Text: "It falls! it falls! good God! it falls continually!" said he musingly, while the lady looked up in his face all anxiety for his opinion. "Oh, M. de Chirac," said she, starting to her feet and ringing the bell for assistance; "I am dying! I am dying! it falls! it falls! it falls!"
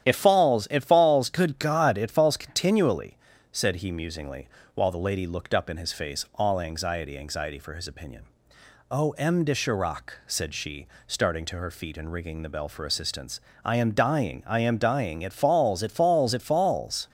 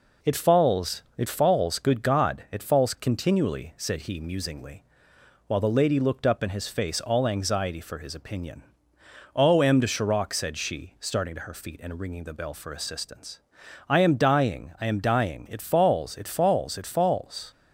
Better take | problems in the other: second | starts louder than the rest; strong; until 1.1 s; 10.5 dB // says "anxiety" twice; at 7.1 s

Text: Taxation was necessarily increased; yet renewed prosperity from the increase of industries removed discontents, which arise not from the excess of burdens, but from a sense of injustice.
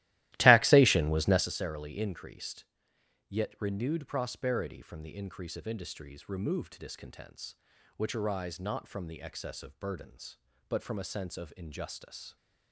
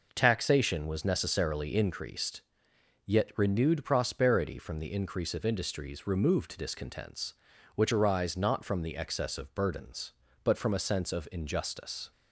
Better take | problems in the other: second | starts louder than the rest; strong; until 1.5 s; 16 dB

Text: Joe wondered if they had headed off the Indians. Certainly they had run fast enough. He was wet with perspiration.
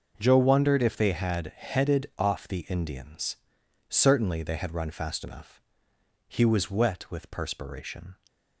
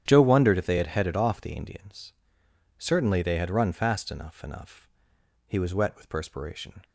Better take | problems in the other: first | starts louder than the rest; strong; until 1.0 s; 10 dB // says "enough" twice; at 4.4 s

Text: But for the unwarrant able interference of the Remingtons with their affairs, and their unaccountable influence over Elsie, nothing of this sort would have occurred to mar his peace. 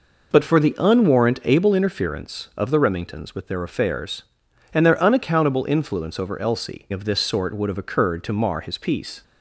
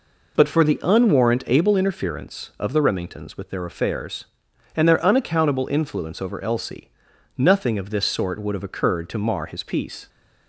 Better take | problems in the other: second | skips "nothing"; at 6.9 s

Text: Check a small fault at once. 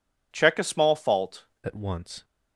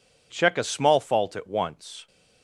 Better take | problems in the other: second | changes voice at "at"; from 1.6 s on; 0.6 s long

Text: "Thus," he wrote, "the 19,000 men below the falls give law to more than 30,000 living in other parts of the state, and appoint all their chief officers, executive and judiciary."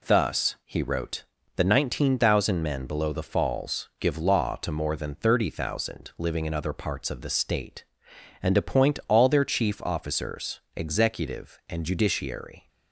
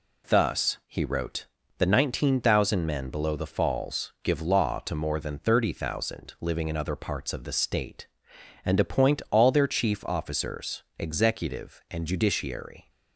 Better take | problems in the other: neither | none

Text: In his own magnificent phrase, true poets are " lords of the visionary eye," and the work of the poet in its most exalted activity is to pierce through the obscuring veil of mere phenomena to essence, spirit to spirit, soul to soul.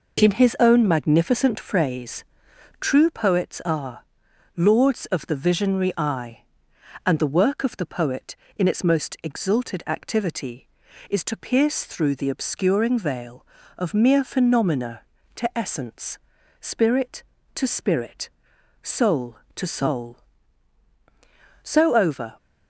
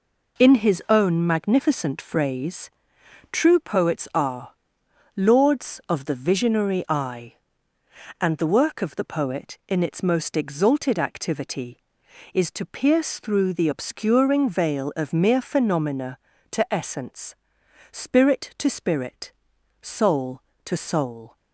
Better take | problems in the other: second | goes on to say "So over"; noticeable; from 21.6 s on; 0.76 s long

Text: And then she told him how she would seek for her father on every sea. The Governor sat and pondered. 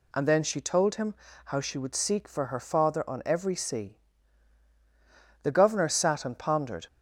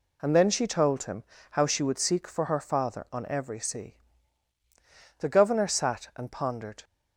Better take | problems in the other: neither | pauses between "him" and "how"; slight; the same in both

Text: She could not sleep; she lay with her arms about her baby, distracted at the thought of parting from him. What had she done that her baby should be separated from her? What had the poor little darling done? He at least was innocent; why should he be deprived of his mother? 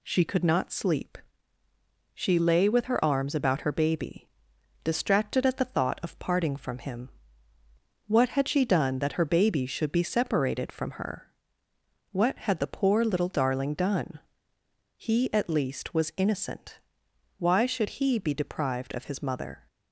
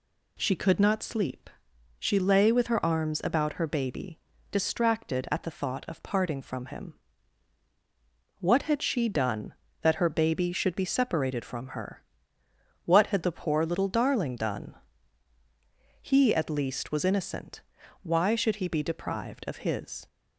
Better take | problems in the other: first | stops before "mother"; at 20.0 s

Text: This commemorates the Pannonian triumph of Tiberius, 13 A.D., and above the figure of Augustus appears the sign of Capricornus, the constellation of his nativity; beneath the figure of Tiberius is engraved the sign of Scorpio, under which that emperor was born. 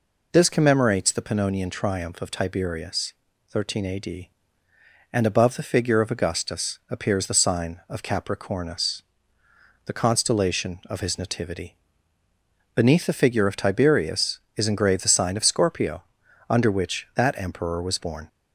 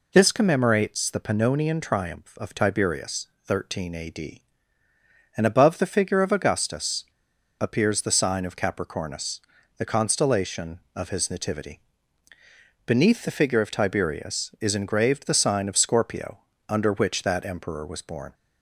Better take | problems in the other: first | pauses between "Augustus" and "appears"; noticeable; at 7.0 s; 0.55 s long

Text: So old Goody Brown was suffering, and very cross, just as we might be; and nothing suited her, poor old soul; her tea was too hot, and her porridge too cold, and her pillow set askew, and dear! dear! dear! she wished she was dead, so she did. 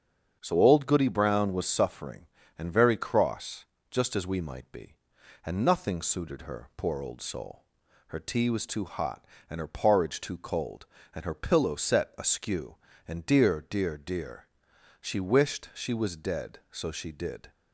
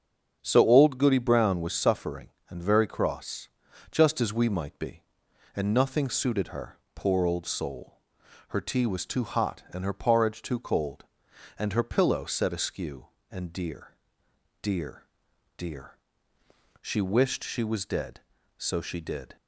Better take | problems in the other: neither | starts louder than the rest; strong; the same in both

